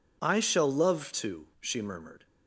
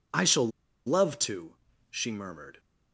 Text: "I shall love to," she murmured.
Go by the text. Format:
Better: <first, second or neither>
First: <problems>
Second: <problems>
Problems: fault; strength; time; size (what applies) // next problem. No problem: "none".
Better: first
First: none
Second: pauses between "shall" and "love"; at 0.4 s; 0.38 s long